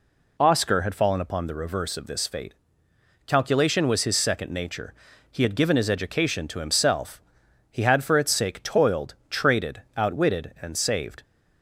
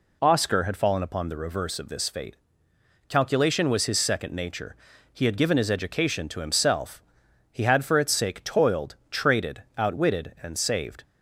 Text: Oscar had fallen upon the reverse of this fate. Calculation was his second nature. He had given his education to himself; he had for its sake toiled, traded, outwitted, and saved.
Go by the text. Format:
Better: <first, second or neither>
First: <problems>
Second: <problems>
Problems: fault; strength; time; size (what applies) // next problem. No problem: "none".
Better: neither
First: none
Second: none